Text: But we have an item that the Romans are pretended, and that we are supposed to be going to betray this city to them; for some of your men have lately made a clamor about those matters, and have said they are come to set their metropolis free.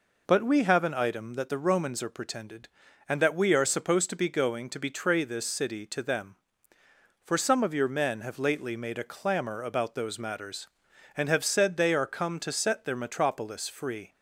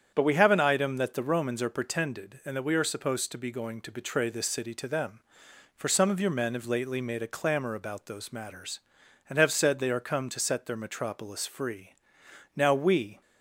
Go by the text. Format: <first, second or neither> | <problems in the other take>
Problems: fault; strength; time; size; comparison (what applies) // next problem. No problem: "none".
first | starts louder than the rest; strong; until 1.1 s; 8.5 dB // goes on to say "Now we"; noticeable; from 12.5 s on; 0.66 s long